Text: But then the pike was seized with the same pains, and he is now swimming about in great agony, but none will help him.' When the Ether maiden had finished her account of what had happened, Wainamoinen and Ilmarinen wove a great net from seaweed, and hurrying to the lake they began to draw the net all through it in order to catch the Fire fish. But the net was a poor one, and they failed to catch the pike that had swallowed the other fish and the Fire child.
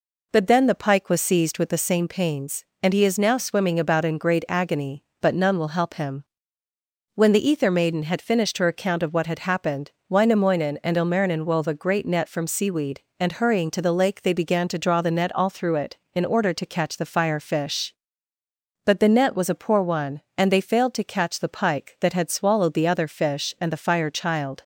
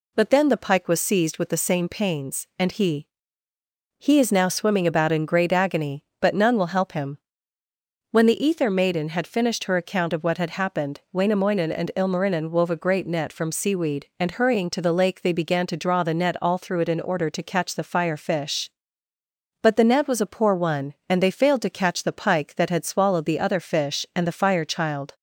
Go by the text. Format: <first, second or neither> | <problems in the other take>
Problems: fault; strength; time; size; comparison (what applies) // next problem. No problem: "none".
first | says "he" twice; at 3.9 s